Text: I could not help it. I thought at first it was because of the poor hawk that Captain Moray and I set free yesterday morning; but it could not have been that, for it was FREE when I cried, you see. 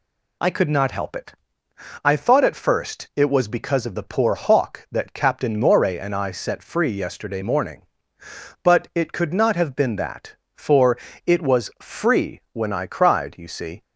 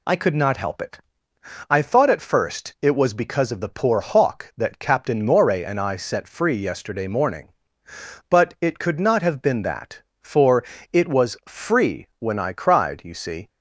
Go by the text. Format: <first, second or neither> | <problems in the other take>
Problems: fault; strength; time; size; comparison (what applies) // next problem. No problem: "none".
neither | pauses between "for" and "it"; slight; the same in both